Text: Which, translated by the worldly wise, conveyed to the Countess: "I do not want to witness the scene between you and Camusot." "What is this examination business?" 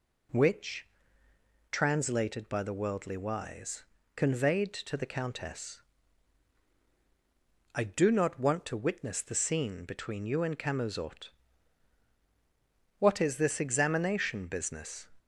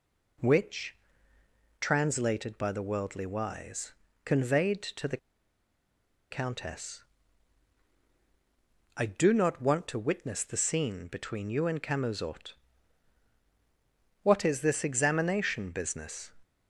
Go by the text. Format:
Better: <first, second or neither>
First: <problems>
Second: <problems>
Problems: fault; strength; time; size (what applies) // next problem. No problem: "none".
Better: first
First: none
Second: pauses between "the" and "Countess"; at 5.1 s; 1.1 s long